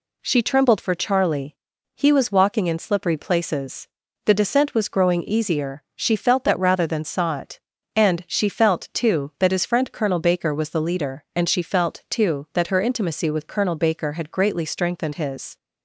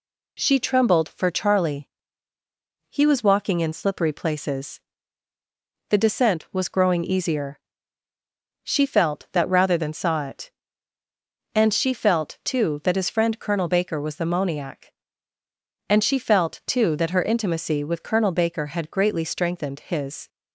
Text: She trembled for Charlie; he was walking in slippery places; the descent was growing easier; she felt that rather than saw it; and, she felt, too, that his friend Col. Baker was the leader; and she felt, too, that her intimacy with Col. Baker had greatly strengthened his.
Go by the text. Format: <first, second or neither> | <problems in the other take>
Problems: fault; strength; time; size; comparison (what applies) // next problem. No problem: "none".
first | says "moniac" for "leader"; at 14.2 s